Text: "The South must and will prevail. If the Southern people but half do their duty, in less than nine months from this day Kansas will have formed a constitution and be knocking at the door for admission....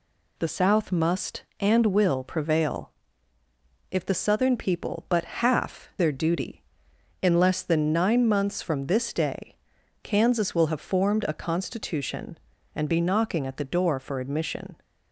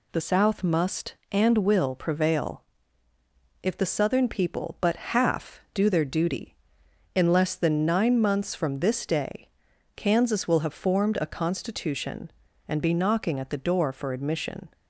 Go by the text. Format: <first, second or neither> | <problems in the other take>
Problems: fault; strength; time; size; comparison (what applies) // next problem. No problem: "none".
second | skips "do"; at 5.9 s // pauses between "day" and "Kansas"; noticeable; at 9.5 s; 0.46 s long; noticeable in the second